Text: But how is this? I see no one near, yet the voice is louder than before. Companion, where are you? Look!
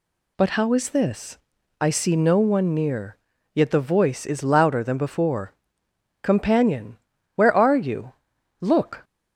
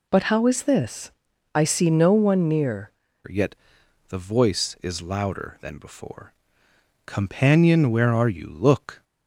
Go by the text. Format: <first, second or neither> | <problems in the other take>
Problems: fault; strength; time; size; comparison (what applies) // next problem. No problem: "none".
first | changes voice at "yet"; from 3.2 s on; 5.8 s long // pauses between "yet" and "the"; noticeable; at 3.5 s; 0.54 s long